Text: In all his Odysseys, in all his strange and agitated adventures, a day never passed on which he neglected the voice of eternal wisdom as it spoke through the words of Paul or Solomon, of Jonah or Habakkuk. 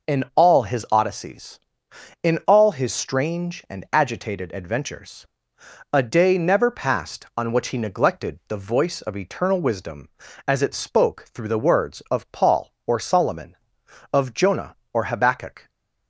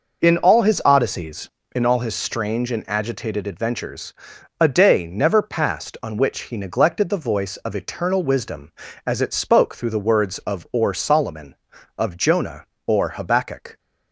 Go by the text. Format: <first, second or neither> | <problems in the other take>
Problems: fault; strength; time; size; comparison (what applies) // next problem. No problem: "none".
first | skips "Paul"; at 10.6 s